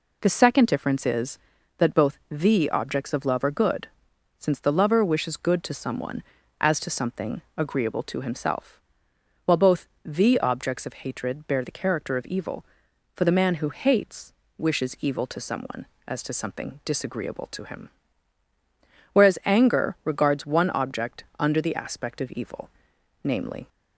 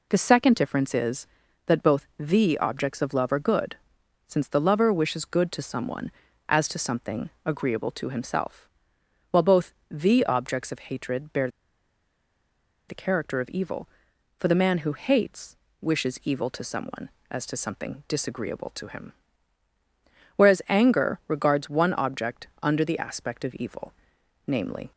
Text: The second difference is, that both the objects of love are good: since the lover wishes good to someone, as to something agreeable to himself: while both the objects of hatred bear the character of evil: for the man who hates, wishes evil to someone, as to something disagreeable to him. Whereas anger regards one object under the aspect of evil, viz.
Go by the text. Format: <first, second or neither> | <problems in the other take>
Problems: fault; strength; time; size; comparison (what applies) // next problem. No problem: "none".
first | pauses between "something" and "agreeable"; slight; at 7.2 s; 0.16 s long; slight in the first // pauses between "both" and "the"; slight; at 9.7 s; 0.18 s long; slight in the first // pauses between "bear" and "the"; strong; at 11.4 s; 1.4 s long // pauses between "object" and "under"; slight; at 22.4 s; 0.16 s long; slight in the first